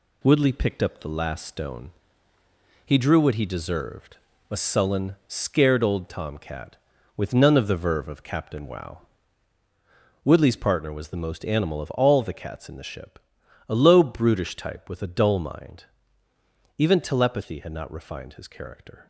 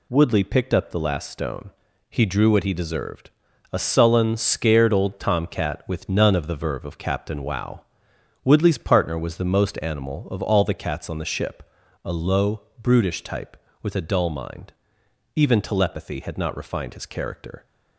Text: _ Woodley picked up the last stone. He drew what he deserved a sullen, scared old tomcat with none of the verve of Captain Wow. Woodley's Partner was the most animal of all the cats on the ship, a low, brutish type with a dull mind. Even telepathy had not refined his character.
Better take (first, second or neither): second